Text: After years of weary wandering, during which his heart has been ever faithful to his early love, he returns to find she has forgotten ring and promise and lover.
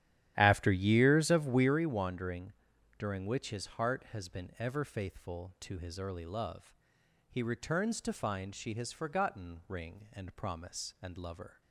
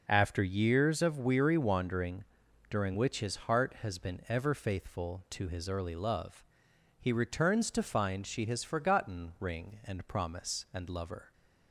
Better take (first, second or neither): second